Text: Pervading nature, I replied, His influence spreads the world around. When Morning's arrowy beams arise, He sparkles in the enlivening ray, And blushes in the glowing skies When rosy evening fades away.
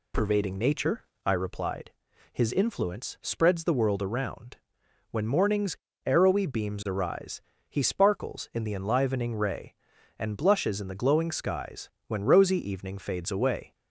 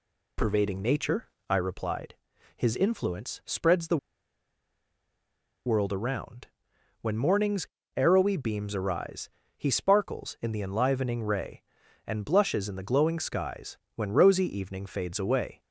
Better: first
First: pauses between "Morning's" and "arrowy"; slight; at 5.7 s; 0.30 s long // pauses between "skies" and "When"; slight; at 11.8 s; 0.20 s long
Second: pauses between "the" and "world"; strong; at 3.9 s; 1.6 s long // pauses between "Morning's" and "arrowy"; slight; at 7.6 s; 0.30 s long // pauses between "skies" and "When"; slight; at 13.7 s; 0.20 s long

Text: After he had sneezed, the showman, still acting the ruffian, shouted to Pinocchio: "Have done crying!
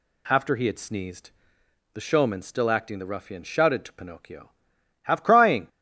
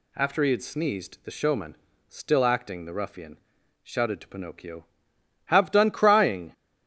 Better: second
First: skips "done"; at 5.2 s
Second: none

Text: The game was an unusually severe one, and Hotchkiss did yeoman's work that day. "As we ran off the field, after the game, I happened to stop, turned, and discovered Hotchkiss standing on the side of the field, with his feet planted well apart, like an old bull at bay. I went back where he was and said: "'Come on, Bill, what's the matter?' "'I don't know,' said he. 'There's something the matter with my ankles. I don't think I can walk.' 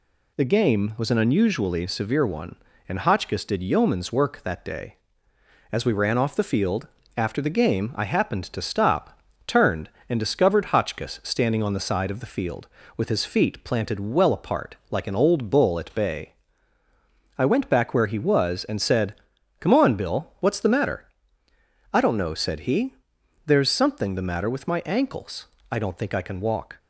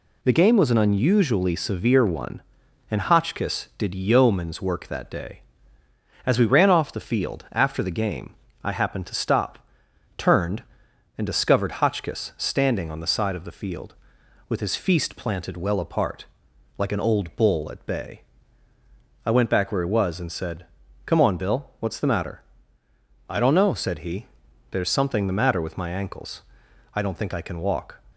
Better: first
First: none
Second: says "feast" for "feet"; at 14.7 s

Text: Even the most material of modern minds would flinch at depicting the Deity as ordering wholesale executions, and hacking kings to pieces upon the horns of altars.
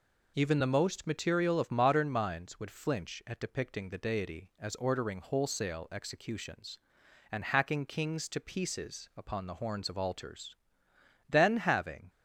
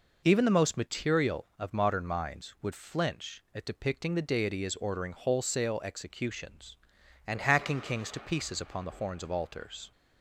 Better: second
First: goes on to say "Then having"; noticeable; from 11.2 s on; 0.80 s long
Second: none

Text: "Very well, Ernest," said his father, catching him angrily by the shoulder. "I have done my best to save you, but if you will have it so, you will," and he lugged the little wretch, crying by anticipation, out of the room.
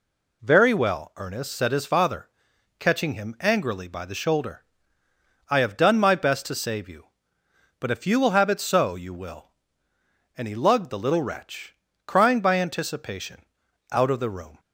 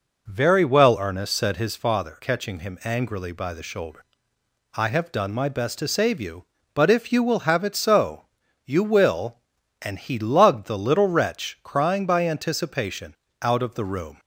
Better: first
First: none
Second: starts louder than the rest; noticeable; until 1.8 s; 5 dB

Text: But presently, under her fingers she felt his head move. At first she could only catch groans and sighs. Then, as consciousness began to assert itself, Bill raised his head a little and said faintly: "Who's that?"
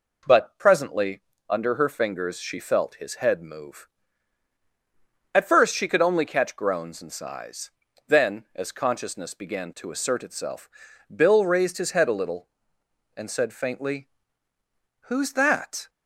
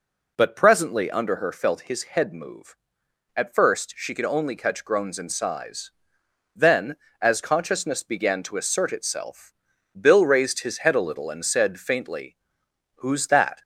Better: first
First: none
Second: skips "fingers she"; at 1.5 s

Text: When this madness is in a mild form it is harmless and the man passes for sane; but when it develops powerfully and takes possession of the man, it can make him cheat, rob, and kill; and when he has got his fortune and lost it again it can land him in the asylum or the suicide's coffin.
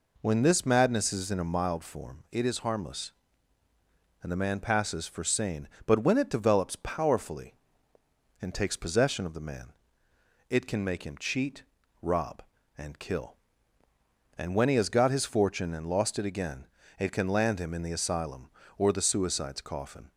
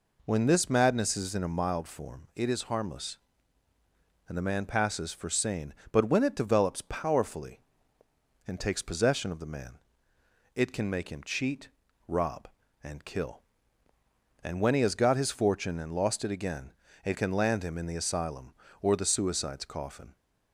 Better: neither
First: pauses between "again" and "it"; slight; at 16.6 s; 0.32 s long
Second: pauses between "again" and "it"; slight; at 16.7 s; 0.32 s long

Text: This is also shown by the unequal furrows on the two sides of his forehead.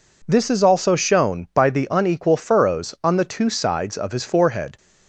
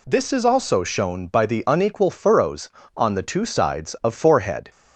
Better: first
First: none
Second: skips "his"; at 4.1 s

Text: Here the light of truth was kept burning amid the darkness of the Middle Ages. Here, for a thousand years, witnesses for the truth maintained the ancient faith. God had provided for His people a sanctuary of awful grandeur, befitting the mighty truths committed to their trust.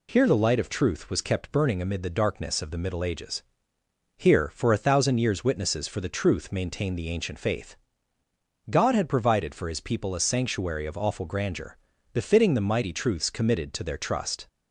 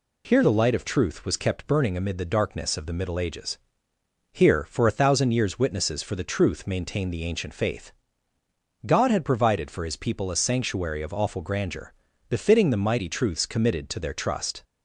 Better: neither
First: none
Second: none

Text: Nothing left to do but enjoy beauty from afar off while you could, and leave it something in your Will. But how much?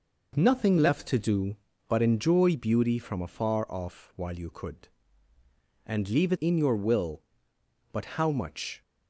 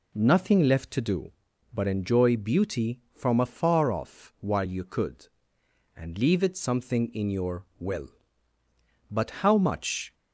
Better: second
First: skips "something"; at 6.3 s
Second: none

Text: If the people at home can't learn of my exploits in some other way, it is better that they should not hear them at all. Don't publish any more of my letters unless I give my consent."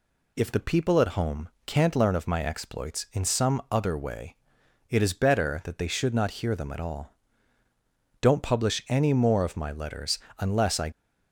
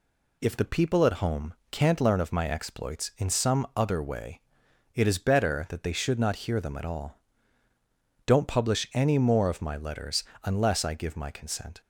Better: second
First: pauses between "home" and "can't"; slight; at 1.4 s; 0.16 s long // pauses between "letters" and "unless"; slight; at 10.1 s; 0.20 s long // stops before "give my consent"; at 10.9 s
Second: pauses between "home" and "can't"; slight; at 1.5 s; 0.16 s long // pauses between "letters" and "unless"; slight; at 10.2 s; 0.20 s long

